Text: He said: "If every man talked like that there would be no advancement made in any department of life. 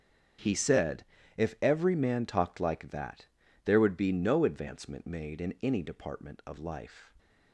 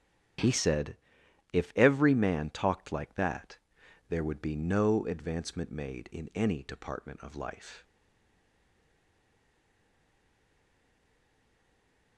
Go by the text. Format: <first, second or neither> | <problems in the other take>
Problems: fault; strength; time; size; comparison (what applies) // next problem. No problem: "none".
first | starts louder than the rest; strong; until 1.9 s; 9 dB; strong in the first // pauses between "that" and "there"; noticeable; at 3.5 s; 0.50 s long; also in the first // stays silent after the last word; strong; from 7.8 s on; 4.3 s long